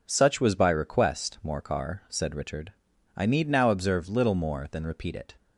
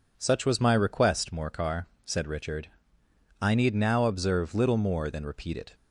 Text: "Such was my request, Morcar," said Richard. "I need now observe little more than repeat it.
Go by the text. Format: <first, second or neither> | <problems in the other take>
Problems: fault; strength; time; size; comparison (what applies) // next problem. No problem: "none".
second | says "by" for "my"; at 0.5 s